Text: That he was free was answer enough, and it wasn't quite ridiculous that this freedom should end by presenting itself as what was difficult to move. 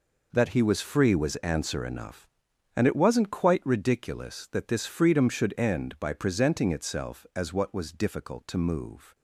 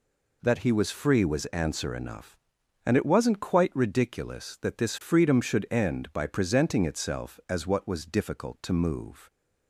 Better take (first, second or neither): second